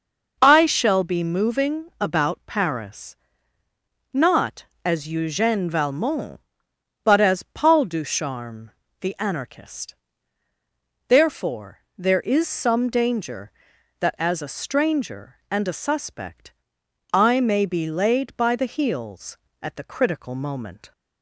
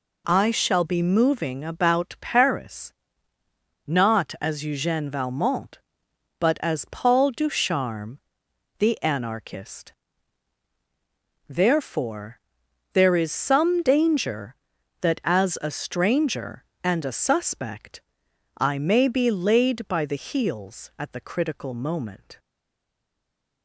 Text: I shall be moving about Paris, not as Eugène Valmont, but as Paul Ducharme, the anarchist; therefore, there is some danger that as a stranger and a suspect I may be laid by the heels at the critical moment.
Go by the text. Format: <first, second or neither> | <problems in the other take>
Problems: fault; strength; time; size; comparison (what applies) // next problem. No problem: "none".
first | pauses between "suspect" and "I"; noticeable; at 18.0 s; 0.56 s long; noticeable in the first // stays silent after the last word; noticeable; from 22.3 s on; 1.3 s long